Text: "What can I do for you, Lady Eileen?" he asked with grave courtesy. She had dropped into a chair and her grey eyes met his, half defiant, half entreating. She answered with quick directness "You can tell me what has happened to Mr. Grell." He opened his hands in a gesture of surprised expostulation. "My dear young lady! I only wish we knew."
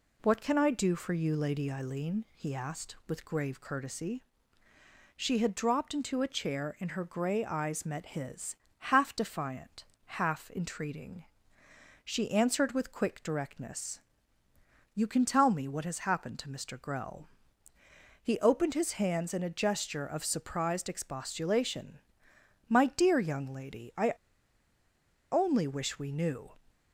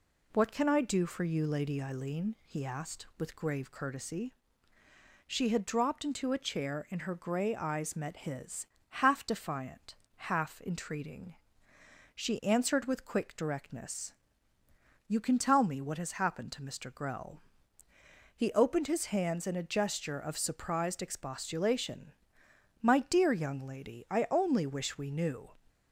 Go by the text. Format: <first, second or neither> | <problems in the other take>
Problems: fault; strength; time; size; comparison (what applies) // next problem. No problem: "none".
second | pauses between "directness" and "You"; noticeable; at 13.9 s; 0.94 s long; noticeable in the second // pauses between "I" and "only"; at 24.1 s; 1.2 s long